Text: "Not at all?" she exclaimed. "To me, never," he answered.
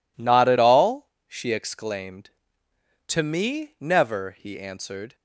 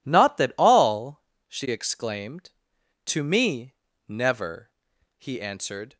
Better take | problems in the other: first | says "that" for "at"; at 0.3 s

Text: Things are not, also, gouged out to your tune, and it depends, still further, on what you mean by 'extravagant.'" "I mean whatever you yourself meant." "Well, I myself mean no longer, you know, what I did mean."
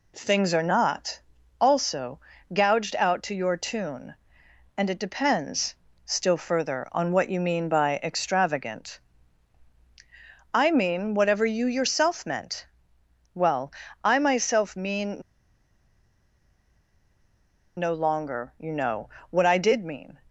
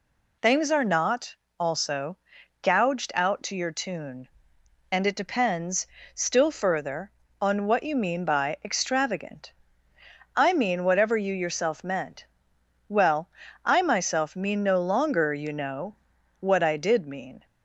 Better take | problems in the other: second | pauses between "mean" and "no"; strong; at 15.2 s; 2.5 s long

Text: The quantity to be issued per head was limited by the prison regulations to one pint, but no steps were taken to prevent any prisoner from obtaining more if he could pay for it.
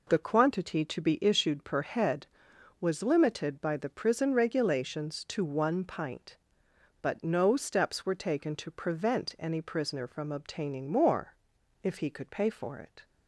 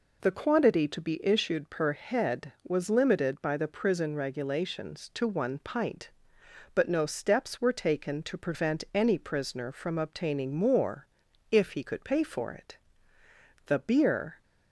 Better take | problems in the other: first | pauses between "more" and "if"; at 11.0 s; 0.44 s long; noticeable in the first // goes on to say "The beer"; noticeable; from 13.6 s on; 0.76 s long

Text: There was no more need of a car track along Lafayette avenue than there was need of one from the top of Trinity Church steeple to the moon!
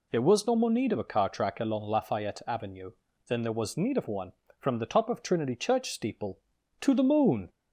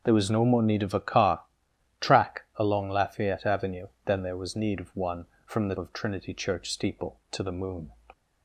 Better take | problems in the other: first | pauses between "car" and "track"; noticeable; at 1.4 s; 0.58 s long // skips "top"; at 5.7 s

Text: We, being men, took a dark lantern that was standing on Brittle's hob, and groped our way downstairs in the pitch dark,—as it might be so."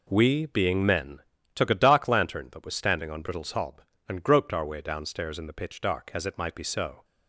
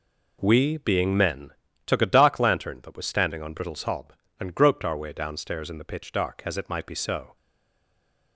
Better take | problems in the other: first | stays silent after the last word; from 7.3 s on; 1.0 s long

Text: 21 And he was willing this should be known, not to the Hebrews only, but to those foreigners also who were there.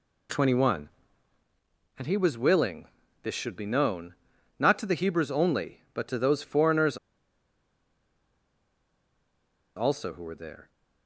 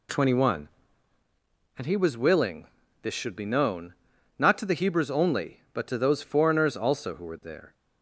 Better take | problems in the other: second | pauses between "willing" and "this"; slight; at 2.8 s; 0.36 s long; slight in the second // pauses between "foreigners" and "also"; strong; at 6.9 s; 2.7 s long

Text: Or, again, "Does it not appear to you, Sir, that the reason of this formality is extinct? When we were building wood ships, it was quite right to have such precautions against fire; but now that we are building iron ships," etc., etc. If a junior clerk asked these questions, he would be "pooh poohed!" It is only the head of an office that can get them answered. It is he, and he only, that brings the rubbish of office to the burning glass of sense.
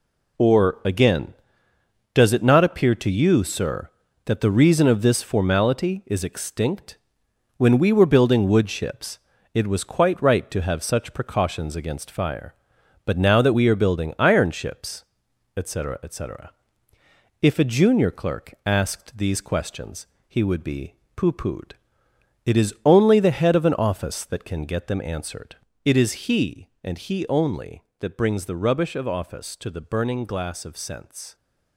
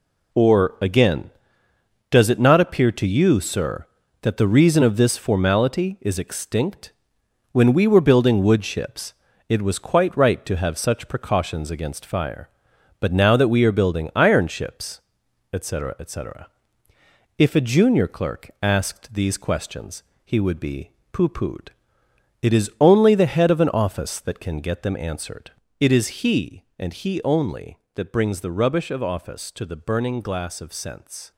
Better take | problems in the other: neither | pauses between "be" and "pooh"; slight; the same in both

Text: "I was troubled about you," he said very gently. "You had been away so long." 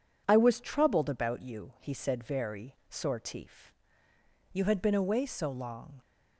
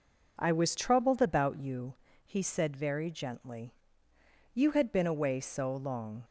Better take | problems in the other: second | says "sortif" for "gently"; at 2.9 s

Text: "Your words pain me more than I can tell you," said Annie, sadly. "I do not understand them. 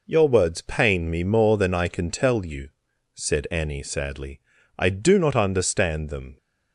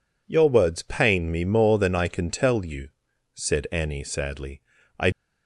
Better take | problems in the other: first | stops before "do not understand them"; at 5.1 s

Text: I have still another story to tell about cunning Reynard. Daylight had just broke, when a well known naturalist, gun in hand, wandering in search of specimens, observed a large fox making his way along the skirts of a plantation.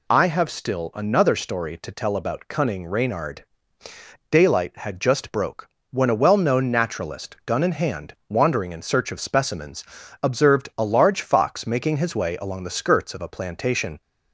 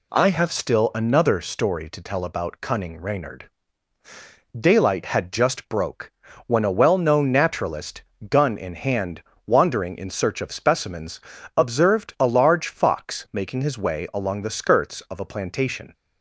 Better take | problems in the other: neither | none

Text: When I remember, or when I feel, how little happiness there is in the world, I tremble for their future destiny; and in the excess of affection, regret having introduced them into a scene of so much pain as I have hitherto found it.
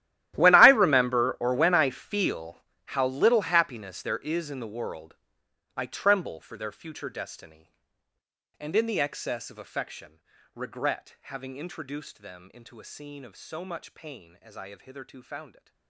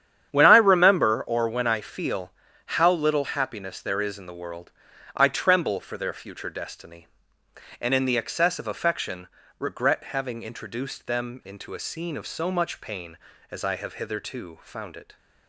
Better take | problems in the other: second | gets quieter; strong; throughout; 21 dB // starts louder than the rest; strong; until 1.3 s; 14 dB; strong in the second

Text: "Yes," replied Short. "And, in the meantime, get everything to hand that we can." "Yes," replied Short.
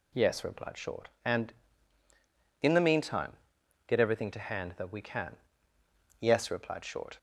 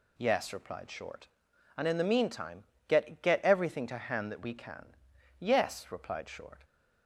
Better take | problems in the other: first | says "get" twice; at 3.1 s

